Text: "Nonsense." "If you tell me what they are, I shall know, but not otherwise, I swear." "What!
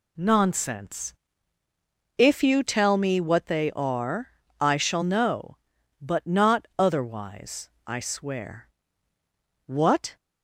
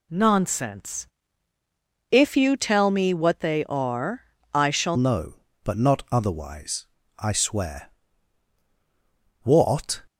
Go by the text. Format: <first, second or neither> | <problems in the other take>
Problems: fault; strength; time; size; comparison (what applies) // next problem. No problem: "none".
first | changes voice at "know"; from 4.9 s on; 5.1 s long